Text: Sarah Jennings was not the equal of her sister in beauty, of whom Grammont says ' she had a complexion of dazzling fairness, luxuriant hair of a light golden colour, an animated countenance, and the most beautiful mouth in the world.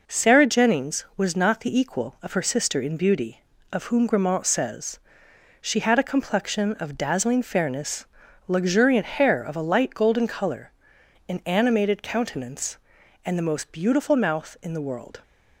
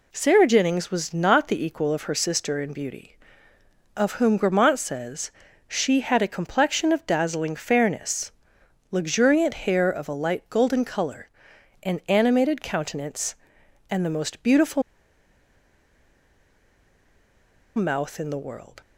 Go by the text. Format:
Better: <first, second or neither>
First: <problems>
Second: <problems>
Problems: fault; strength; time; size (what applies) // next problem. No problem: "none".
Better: first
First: none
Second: pauses between "beautiful" and "mouth"; strong; at 14.8 s; 2.9 s long